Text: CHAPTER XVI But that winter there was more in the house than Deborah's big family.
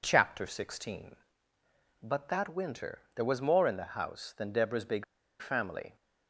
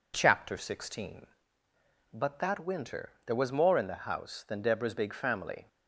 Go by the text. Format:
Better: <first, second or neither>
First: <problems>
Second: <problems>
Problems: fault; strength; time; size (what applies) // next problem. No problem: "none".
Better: second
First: pauses between "winter" and "there"; slight; at 2.9 s; 0.18 s long // pauses between "big" and "family"; at 5.0 s; 0.36 s long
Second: pauses between "winter" and "there"; slight; at 3.0 s; 0.18 s long